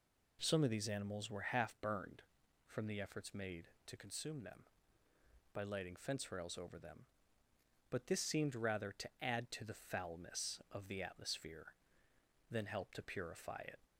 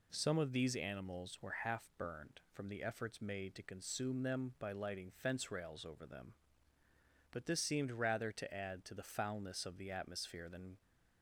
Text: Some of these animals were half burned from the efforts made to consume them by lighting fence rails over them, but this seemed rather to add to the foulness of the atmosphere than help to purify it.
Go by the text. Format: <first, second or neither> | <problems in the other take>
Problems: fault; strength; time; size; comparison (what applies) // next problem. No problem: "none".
first | stops before "help to purify it"; at 10.8 s